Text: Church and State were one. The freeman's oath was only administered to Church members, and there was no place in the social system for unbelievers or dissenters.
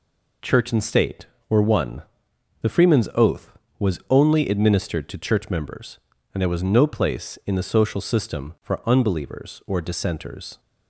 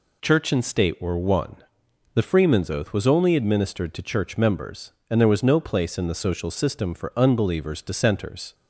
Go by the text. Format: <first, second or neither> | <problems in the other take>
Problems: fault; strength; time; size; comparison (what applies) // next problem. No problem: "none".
first | skips "or"; at 7.7 s